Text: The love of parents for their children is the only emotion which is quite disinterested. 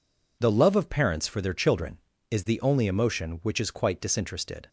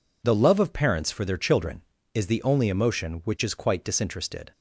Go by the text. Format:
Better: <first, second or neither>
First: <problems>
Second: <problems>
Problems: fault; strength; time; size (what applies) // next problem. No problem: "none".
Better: neither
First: none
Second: none